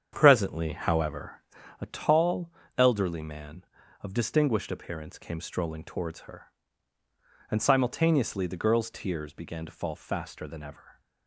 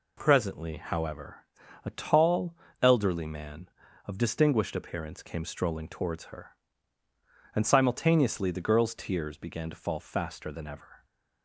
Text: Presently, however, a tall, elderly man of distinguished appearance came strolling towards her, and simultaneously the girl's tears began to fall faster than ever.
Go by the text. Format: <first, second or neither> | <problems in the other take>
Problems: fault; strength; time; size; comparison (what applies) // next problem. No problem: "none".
second | starts louder than the rest; strong; until 1.7 s; 8 dB